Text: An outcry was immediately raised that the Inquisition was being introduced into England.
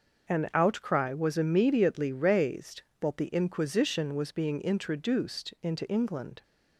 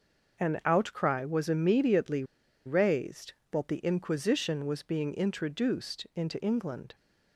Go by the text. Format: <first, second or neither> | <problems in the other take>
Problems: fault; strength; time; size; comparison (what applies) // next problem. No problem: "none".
first | starts louder than the rest; noticeable; until 1.4 s; 6 dB; also in the first // pauses between "immediately" and "raised"; at 2.2 s; 0.42 s long